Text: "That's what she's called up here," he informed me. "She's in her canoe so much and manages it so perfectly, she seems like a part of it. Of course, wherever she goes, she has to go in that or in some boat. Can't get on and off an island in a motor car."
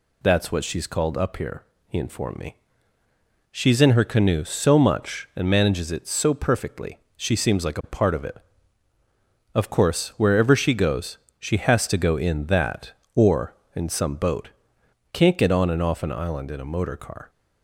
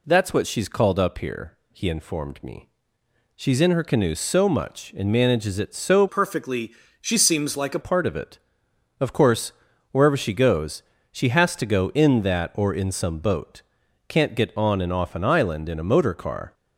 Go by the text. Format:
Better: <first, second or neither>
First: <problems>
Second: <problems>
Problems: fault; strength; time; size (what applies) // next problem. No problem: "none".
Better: first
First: none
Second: changes voice from "perfectly" to "a"; from 6.0 to 7.8 s; 1.8 s long